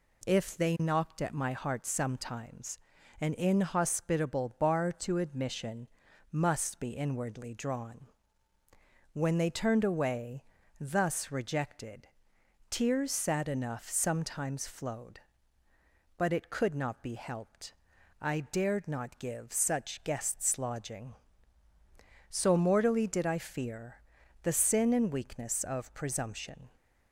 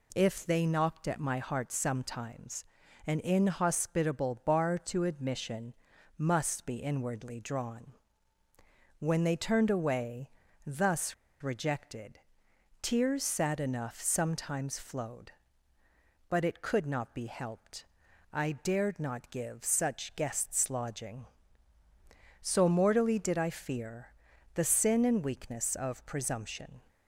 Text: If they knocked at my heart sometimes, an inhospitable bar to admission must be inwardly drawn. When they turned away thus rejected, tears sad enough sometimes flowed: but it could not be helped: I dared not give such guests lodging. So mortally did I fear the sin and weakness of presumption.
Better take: first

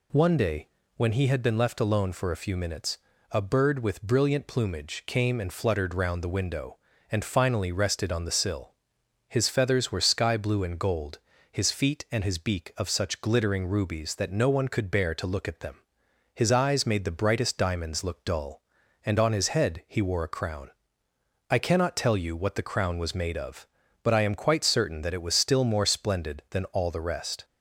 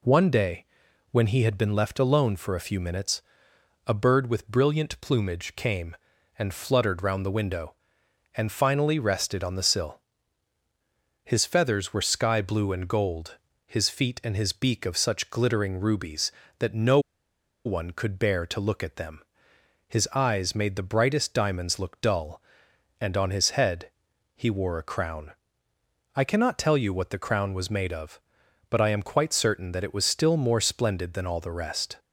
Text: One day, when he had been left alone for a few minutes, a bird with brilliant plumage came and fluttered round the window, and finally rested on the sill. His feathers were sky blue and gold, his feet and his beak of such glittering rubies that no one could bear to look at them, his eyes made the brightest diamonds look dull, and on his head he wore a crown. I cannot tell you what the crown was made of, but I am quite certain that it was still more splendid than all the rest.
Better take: first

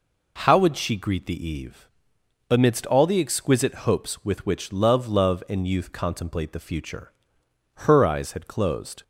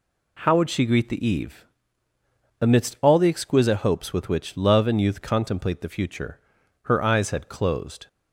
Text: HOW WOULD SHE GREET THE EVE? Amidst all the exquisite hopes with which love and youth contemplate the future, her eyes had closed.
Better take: second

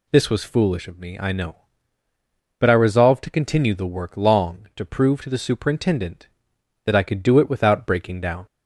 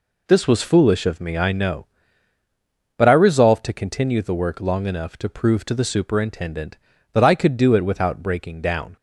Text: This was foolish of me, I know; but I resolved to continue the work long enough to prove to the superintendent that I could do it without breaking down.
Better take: second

